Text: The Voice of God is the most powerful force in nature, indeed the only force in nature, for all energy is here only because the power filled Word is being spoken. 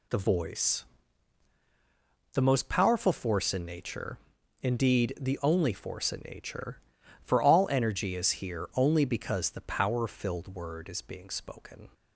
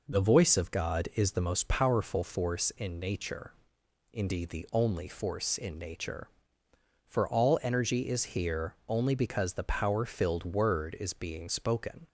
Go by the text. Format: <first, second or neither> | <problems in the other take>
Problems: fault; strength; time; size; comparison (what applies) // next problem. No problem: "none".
second | skips "of God is"; at 1.5 s